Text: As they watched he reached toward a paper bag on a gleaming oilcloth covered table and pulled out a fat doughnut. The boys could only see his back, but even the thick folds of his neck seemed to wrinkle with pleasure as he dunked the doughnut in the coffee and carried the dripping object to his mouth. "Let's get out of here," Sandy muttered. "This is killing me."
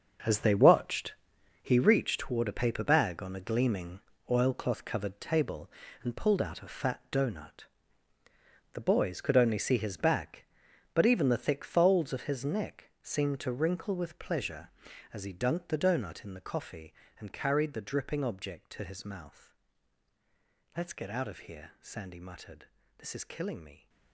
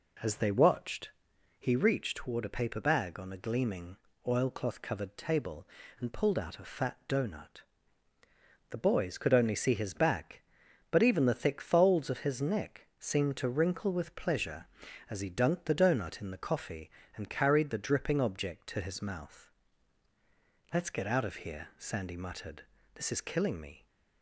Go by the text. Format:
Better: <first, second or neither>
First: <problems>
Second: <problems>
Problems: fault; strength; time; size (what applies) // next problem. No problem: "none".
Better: second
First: gets quieter; strong; throughout; 11.5 dB // pauses between "watched" and "he"; noticeable; at 1.1 s; 0.50 s long // pauses between "gleaming" and "oilcloth"; slight; at 4.0 s; 0.28 s long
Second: pauses between "watched" and "he"; noticeable; at 1.0 s; 0.50 s long // pauses between "gleaming" and "oilcloth"; slight; at 3.9 s; 0.28 s long